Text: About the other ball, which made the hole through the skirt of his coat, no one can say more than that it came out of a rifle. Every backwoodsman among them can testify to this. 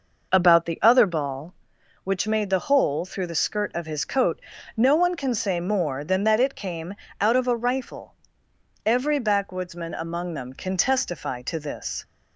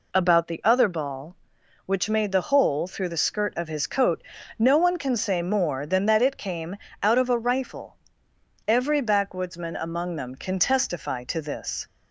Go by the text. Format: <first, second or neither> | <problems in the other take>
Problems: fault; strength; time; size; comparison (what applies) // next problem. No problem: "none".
second | starts louder than the rest; noticeable; until 1.7 s; 5.5 dB // pauses between "came" and "out"; slight; at 6.9 s; 0.28 s long; slight in the second